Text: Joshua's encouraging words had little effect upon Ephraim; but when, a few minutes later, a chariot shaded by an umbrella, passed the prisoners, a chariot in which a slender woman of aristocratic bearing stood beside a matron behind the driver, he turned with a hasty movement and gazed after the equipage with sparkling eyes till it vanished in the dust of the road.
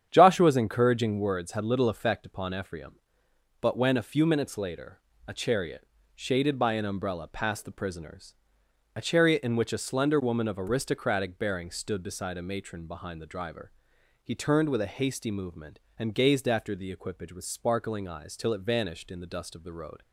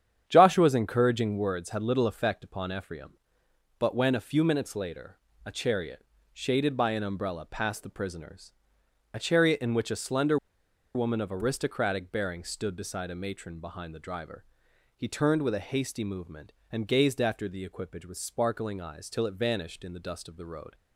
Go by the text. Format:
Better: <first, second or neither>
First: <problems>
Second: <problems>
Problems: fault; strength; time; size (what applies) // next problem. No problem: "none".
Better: first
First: starts louder than the rest; strong; until 1.1 s; 9 dB // pauses between "chariot" and "shaded"; slight; at 5.8 s; 0.28 s long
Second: starts louder than the rest; strong; until 1.2 s; 9 dB // pauses between "chariot" and "shaded"; slight; at 6.0 s; 0.28 s long // pauses between "slender" and "woman"; noticeable; at 10.3 s; 0.58 s long